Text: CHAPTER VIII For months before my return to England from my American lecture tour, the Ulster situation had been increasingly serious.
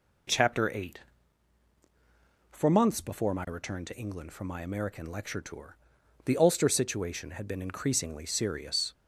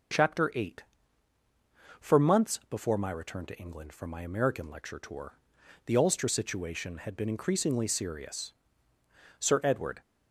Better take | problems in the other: first | goes on to say "Sir Edward"; noticeable; from 9.3 s on; 0.62 s long

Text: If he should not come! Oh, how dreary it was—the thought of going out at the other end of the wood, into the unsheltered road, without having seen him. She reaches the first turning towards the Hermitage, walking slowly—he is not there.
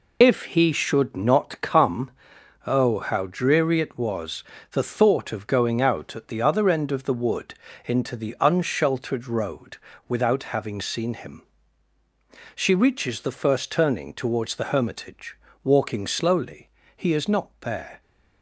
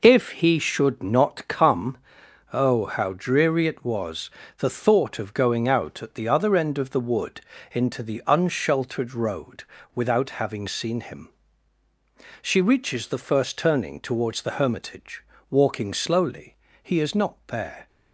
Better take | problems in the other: second | loses the start of "If"; at 0.2 s; 45 ms

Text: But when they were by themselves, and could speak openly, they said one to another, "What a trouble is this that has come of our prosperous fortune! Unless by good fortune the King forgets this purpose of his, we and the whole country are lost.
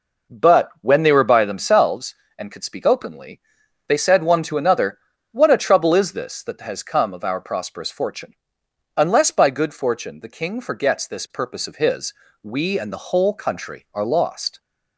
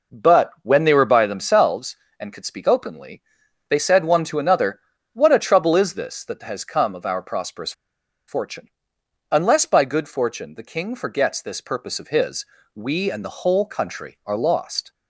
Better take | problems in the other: first | pauses between "prosperous" and "fortune"; noticeable; at 7.7 s; 0.56 s long

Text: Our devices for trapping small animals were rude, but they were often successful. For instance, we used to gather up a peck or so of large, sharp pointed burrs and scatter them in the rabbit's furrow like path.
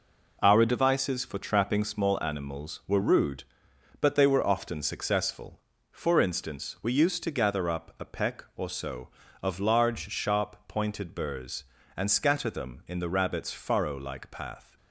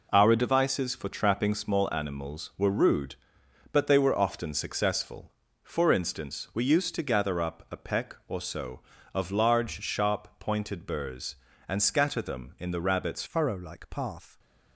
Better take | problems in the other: first | changes voice at "furrow"; from 13.2 s on; 1.1 s long

